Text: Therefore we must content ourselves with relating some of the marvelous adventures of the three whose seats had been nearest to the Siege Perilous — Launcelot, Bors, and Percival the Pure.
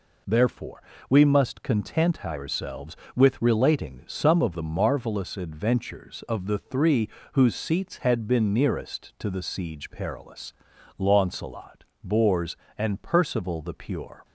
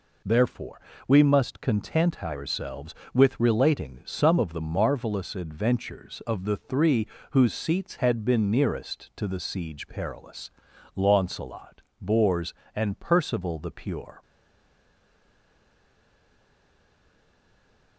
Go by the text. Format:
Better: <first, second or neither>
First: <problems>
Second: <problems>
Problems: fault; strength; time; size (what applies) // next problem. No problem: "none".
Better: first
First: pauses between "Therefore" and "we"; slight; at 0.8 s; 0.26 s long // pauses between "three" and "whose"; slight; at 7.0 s; 0.24 s long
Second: pauses between "Therefore" and "we"; slight; at 0.8 s; 0.26 s long // pauses between "three" and "whose"; slight; at 7.0 s; 0.24 s long // stays silent after the last word; strong; from 14.2 s on; 3.7 s long